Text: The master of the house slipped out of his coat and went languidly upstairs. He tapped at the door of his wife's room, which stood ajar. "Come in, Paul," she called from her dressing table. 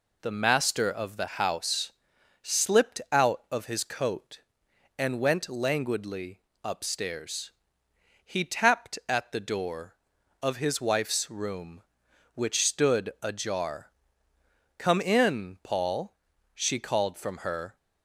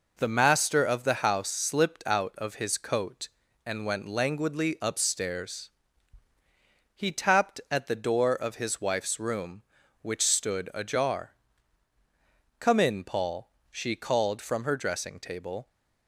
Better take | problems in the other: second | pauses between "house" and "slipped"; noticeable; at 1.9 s; 0.48 s long // pauses between "languidly" and "upstairs"; slight; at 6.3 s; 0.22 s long // stops before "dressing table"; at 17.7 s

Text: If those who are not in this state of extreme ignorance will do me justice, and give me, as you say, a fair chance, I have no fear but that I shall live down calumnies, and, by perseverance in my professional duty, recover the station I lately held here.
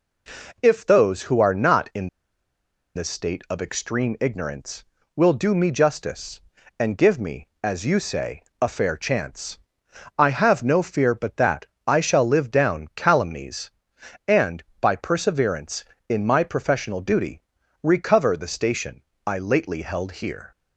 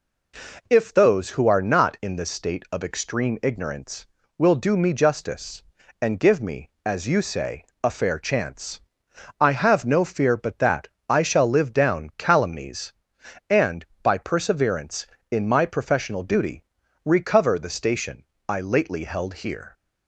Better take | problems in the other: second | pauses between "in" and "this"; noticeable; at 2.0 s; 0.86 s long // pauses between "that" and "I"; slight; at 11.6 s; 0.18 s long; slight in the second // pauses between "station" and "I"; slight; at 19.0 s; 0.24 s long; slight in the second

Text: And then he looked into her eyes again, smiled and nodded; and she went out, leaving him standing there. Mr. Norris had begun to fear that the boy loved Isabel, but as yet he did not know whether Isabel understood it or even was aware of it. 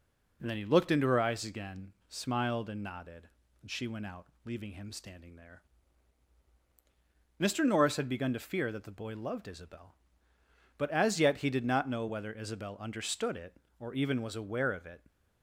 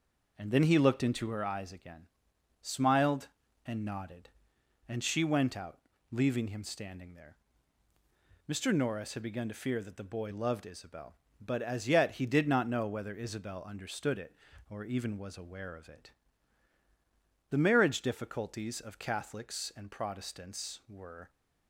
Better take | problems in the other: first | goes on to say "The marriage difficulties of Catholics and Protestants were"; strong; from 17.4 s on; 3.8 s long

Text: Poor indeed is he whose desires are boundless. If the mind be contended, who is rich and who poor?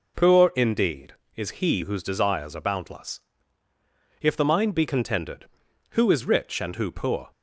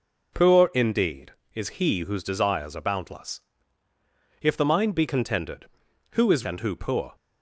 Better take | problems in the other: first | skips "rich"; at 6.4 s

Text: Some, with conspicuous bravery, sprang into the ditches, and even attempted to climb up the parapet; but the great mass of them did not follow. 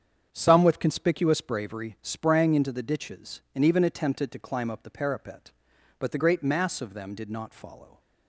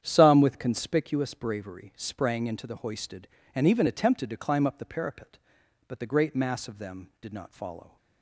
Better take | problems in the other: first | starts louder than the rest; strong; until 1.0 s; 9 dB; strong in the first // says "hoisted" for "ditches"; at 2.7 s

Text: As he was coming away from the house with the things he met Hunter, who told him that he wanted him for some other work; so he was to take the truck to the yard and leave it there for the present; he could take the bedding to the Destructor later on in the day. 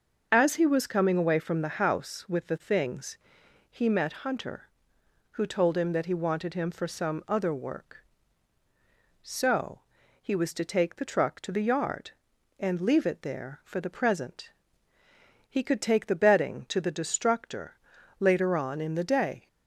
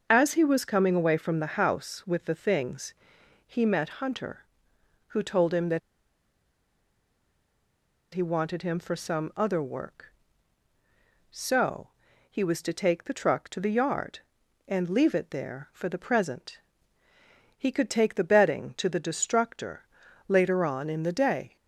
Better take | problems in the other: first | starts louder than the rest; until 1.1 s; 6.5 dB; also in the first // pauses between "things" and "he"; noticeable; at 2.9 s; 0.52 s long; noticeable in the first // pauses between "that" and "he"; strong; at 5.7 s; 2.3 s long // pauses between "so" and "he"; at 11.8 s; 0.40 s long; also in the first // pauses between "Destructor" and "later"; at 19.8 s; 0.42 s long; also in the first

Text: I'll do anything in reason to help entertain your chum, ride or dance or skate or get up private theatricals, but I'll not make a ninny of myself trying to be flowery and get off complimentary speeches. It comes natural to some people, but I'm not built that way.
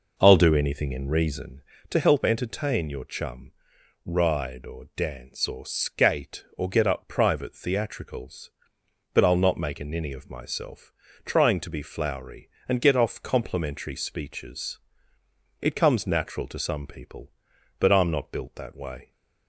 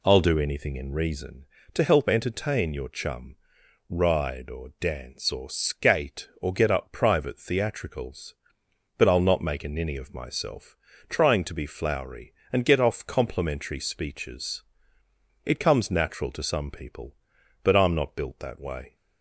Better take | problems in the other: second | starts louder than the rest; noticeable; until 1.9 s; 5 dB // pauses between "myself" and "trying"; slight; at 10.9 s; 0.34 s long; slight in the second

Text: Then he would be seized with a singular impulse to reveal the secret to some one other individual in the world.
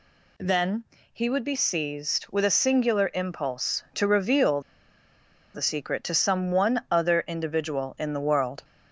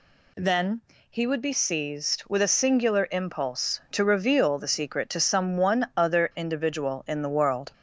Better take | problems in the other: second | pauses between "Then" and "he"; slight; at 0.8 s; 0.30 s long; slight in the second // pauses between "reveal" and "the"; noticeable; at 4.6 s; 0.93 s long

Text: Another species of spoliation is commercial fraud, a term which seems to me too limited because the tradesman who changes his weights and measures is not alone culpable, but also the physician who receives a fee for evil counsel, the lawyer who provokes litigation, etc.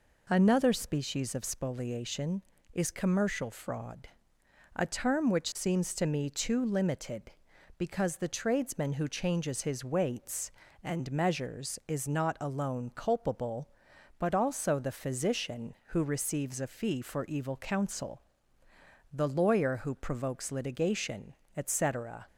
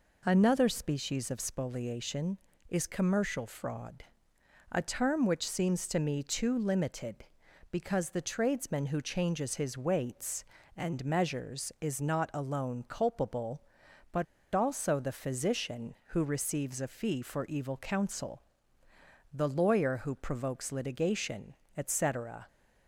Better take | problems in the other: first | pauses between "but" and "also"; slight; at 14.2 s; 0.27 s long

